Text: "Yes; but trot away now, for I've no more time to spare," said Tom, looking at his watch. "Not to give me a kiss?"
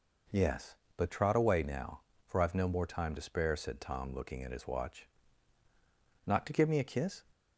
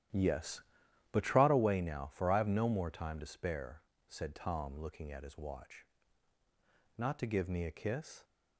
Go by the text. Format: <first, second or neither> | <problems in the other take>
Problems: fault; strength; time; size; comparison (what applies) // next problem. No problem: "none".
first | starts louder than the rest; strong; until 1.6 s; 11.5 dB